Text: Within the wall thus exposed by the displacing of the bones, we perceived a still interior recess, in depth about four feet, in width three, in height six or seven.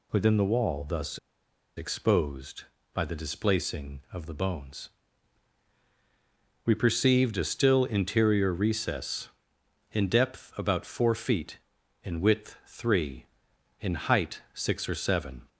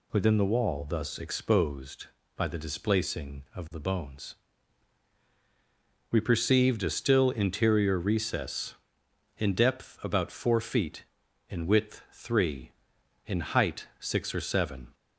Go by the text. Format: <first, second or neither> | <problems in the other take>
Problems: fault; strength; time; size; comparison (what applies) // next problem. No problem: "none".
second | pauses between "thus" and "exposed"; noticeable; at 1.1 s; 0.58 s long